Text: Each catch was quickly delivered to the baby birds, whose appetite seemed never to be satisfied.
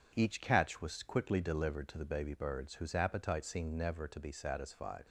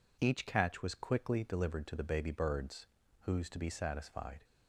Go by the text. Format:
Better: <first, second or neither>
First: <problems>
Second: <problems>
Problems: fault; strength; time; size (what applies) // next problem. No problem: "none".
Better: first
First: none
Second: skips "appetite seemed never"; at 3.4 s